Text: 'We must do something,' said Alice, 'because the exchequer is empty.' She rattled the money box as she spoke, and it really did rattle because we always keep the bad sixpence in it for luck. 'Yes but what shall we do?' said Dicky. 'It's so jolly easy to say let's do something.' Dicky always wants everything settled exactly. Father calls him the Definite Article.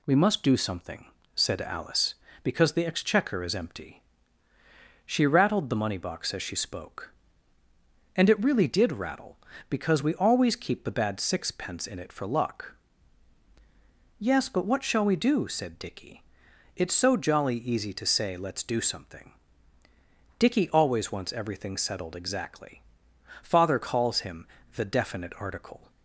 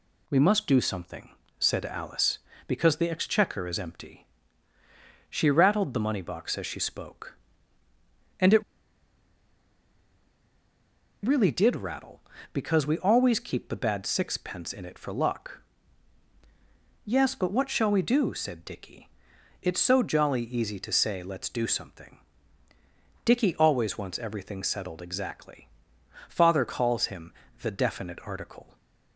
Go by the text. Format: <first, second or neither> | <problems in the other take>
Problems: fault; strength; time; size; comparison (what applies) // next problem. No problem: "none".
first | pauses between "it" and "really"; strong; at 8.6 s; 2.6 s long // pauses between "him" and "the"; slight; at 27.3 s; 0.30 s long; slight in the first